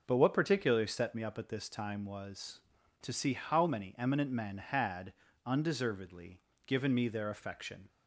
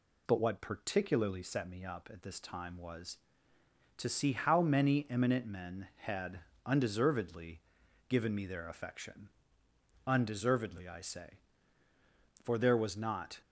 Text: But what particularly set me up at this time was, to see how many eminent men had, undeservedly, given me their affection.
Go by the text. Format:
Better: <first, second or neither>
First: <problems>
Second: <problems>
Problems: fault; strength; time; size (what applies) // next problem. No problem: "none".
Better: first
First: none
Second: goes on to say "Undeservedly I say for there was not"; strong; from 10.0 s on; 3.3 s long